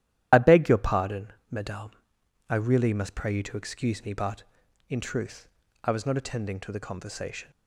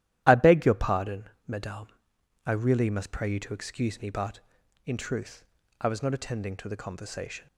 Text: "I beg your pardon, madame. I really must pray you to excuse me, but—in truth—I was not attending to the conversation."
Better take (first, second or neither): second